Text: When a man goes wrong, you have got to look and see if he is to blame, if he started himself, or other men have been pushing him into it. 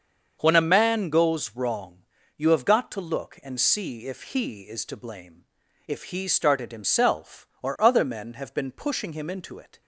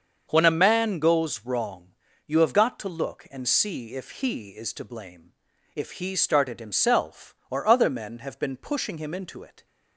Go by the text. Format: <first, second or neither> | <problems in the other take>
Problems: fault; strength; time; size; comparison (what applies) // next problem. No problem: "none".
neither | starts louder than the rest; the same in both